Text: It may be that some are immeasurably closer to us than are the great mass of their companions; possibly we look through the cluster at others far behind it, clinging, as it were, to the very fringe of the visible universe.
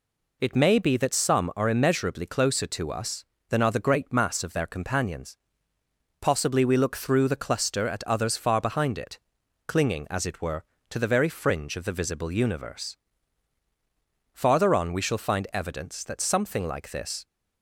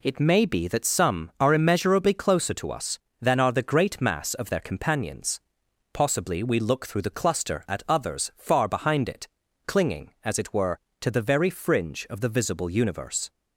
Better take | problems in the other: second | goes on to say "Farther on we shall find evidence that something like this"; strong; from 14.3 s on; 2.9 s long

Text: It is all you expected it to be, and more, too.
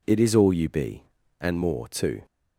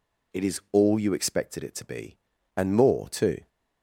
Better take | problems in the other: second | skips "expected it to"; at 0.6 s

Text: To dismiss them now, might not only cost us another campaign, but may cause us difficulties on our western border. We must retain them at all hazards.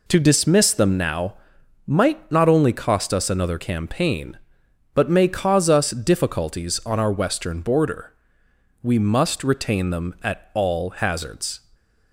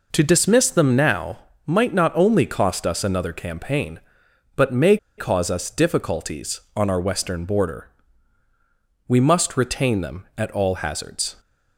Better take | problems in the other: first | pauses between "may" and "cause"; slight; at 4.9 s; 0.21 s long

